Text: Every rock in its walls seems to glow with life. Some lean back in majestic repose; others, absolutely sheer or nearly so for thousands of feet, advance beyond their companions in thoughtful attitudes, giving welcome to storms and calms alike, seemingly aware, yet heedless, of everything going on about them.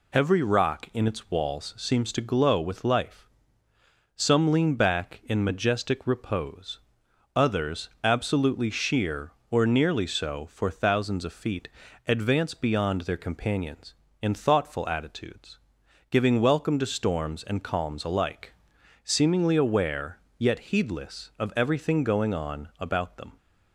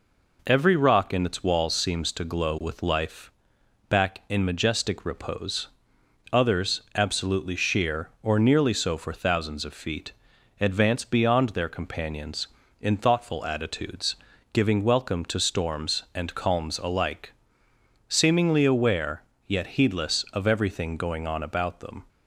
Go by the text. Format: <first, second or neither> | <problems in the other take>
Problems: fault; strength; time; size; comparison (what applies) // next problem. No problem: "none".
first | skips "Some lean"; at 3.5 s